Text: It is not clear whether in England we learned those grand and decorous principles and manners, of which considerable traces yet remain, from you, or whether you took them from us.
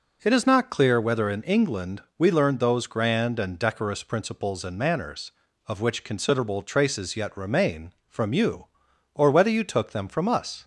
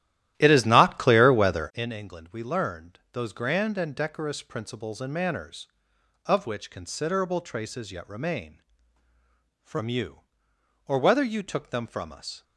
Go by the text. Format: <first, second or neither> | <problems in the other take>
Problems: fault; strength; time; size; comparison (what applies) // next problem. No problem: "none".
first | starts louder than the rest; strong; until 2.0 s; 13.5 dB